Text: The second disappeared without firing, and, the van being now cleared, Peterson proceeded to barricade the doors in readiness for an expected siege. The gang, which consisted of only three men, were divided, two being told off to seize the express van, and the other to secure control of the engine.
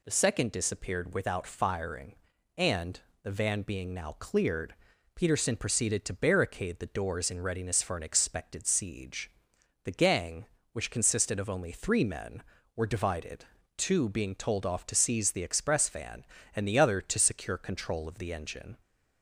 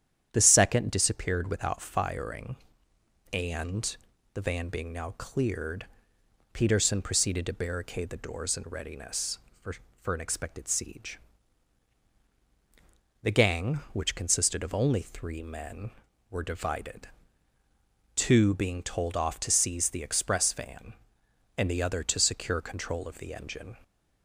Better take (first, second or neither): first